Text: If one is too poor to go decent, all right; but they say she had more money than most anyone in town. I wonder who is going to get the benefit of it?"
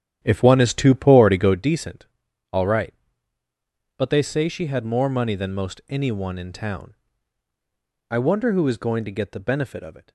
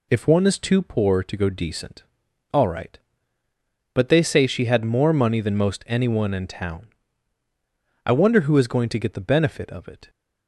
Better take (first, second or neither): second